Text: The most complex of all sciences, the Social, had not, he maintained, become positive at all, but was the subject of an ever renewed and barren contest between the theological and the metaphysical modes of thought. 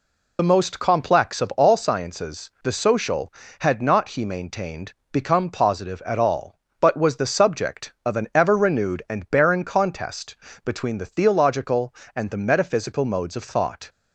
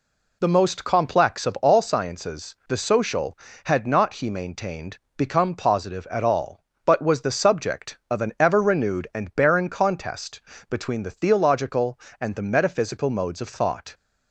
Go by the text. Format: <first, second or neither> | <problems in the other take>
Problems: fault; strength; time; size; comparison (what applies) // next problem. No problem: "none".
second | loses the start of "The"; at 0.3 s; 35 ms // pauses between "contest" and "between"; slight; at 10.3 s; 0.28 s long; slight in the second